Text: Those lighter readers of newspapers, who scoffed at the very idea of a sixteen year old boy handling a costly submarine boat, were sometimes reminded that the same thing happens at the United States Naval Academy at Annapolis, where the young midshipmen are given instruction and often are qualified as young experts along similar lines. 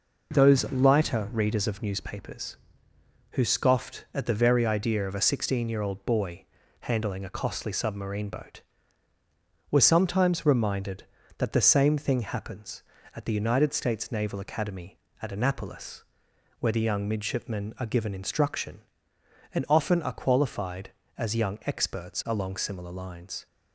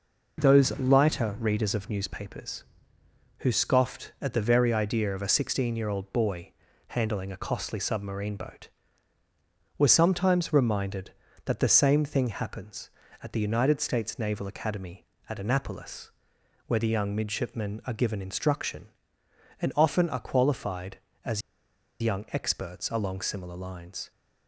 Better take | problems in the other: first | pauses between "boy" and "handling"; slight; at 6.5 s; 0.34 s long; slight in the first // pauses between "as" and "young"; noticeable; at 21.4 s; 0.61 s long

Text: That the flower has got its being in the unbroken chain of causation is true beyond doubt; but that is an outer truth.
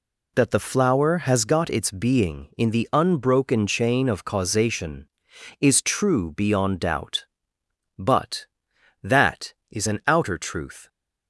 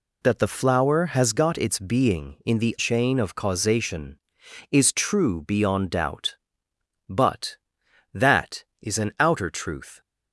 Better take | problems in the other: first | skips "unbroken"; at 2.7 s

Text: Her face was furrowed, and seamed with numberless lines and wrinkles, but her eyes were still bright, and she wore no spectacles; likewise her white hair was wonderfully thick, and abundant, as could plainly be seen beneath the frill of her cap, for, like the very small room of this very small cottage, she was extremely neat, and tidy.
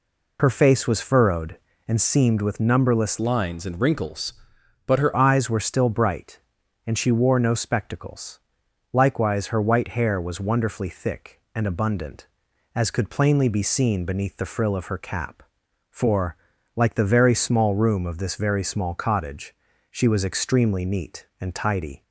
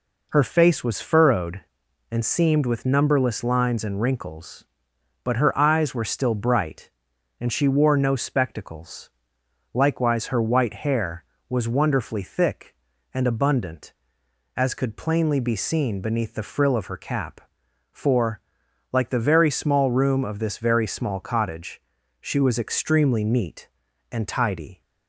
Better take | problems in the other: second | changes voice from "lines" to "her"; from 3.1 to 5.1 s; 2.0 s long

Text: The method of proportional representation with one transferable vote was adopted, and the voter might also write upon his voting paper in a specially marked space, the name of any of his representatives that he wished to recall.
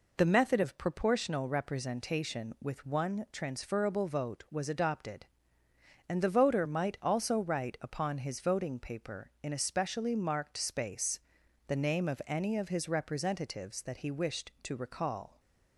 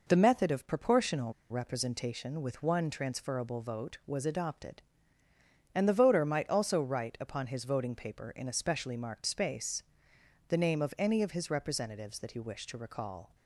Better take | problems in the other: first | pauses between "proportional" and "representation"; slight; at 1.3 s; 0.18 s long

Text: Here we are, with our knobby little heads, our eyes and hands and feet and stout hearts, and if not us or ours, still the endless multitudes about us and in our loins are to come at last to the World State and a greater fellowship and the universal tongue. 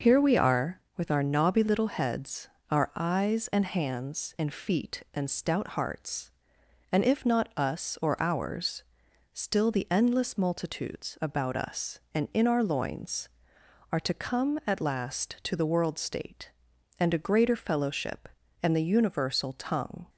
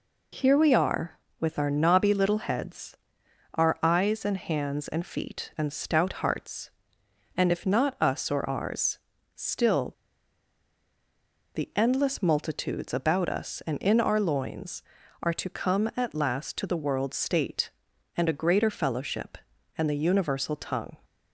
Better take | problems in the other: first | pauses between "still" and "the"; strong; at 9.9 s; 1.6 s long

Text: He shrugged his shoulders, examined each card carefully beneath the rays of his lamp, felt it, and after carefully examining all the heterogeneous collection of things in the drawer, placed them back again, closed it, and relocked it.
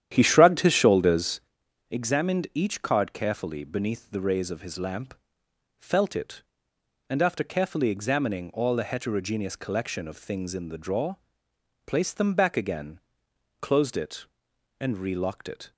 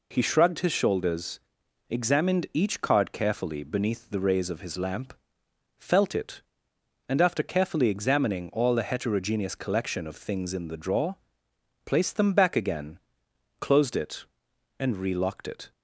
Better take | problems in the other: second | starts louder than the rest; strong; until 1.5 s; 10.5 dB

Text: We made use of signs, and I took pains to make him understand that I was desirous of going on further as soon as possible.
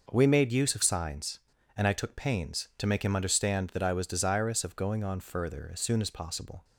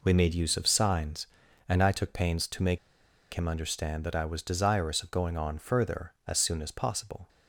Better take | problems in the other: first | pauses between "make" and "him"; noticeable; at 2.7 s; 0.55 s long

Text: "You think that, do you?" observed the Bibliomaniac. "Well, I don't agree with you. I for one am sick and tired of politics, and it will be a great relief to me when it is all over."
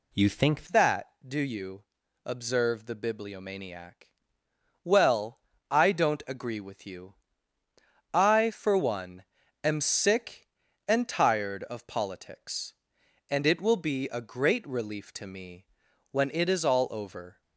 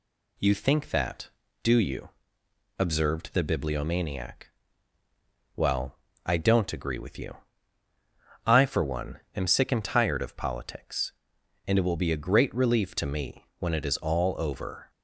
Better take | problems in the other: second | changes voice at "that"; from 0.6 s on; 16.8 s long // pauses between "one" and "am"; slight; at 9.2 s; 0.36 s long // pauses between "me" and "when"; noticeable; at 15.6 s; 0.46 s long

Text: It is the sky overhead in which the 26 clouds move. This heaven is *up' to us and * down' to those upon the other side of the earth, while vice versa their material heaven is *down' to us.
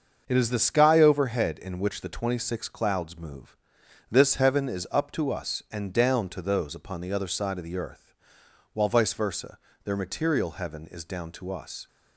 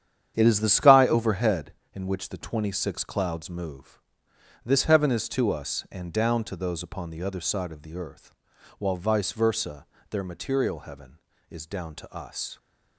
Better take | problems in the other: first | starts louder than the rest; strong; until 1.3 s; 9 dB; also in the first // skips "up"; at 5.2 s // pauses between "versa" and "their"; slight; at 9.8 s; 0.24 s long; slight in the first

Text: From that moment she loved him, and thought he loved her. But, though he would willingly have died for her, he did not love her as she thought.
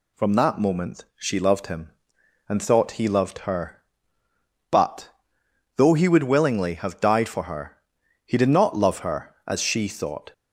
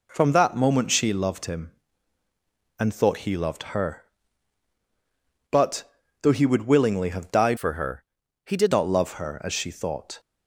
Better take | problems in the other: first | changes voice from "for" to "did"; from 7.5 to 8.7 s; 1.2 s long

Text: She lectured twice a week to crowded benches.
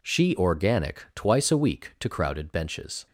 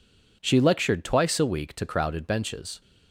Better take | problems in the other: second | says "organic" for "lectured"; at 0.3 s

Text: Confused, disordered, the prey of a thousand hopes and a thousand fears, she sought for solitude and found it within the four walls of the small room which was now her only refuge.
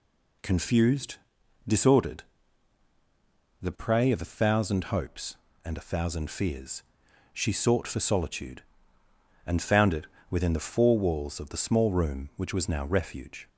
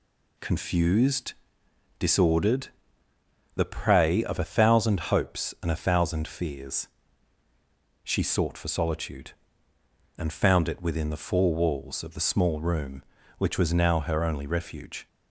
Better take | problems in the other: second | pauses between "it" and "within"; slight; at 10.0 s; 0.22 s long // skips "her only"; at 12.8 s

